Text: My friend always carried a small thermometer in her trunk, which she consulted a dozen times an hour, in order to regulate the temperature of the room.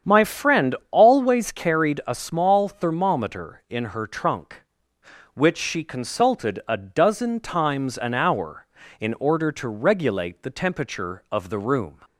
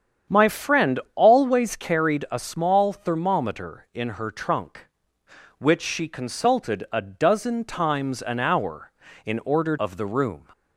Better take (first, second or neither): first